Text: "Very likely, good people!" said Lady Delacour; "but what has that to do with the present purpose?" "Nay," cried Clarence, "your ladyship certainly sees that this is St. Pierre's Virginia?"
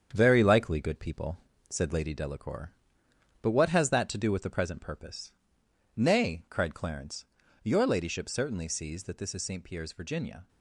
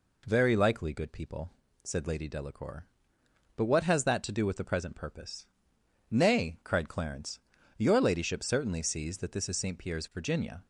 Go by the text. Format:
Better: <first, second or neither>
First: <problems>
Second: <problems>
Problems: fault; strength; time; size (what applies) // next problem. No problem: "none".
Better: second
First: gets quieter; noticeable; throughout; 6 dB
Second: none